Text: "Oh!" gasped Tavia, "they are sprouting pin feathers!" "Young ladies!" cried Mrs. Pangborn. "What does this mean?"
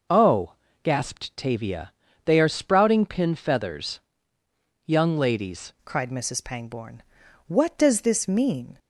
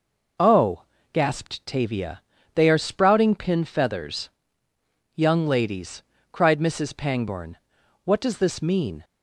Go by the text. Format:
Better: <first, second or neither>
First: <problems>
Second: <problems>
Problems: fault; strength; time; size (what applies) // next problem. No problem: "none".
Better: second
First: changes voice at "cried"; from 5.8 s on; 2.9 s long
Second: none